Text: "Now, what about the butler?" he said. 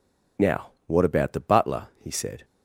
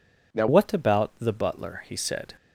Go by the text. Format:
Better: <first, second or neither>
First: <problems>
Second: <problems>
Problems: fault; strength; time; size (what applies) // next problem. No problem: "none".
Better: first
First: none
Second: changes voice at "what"; from 0.4 s on; 1.9 s long